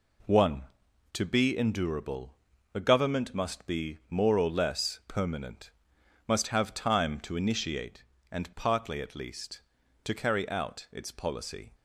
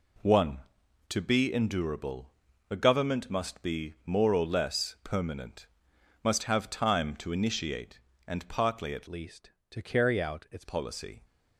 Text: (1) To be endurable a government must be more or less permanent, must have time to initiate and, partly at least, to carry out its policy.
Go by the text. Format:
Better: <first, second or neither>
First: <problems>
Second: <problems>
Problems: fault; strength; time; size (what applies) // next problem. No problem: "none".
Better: first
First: pauses between "endurable" and "a"; at 2.3 s; 0.40 s long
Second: pauses between "endurable" and "a"; at 2.3 s; 0.40 s long // changes voice from "least" to "its"; from 9.0 to 10.6 s; 1.6 s long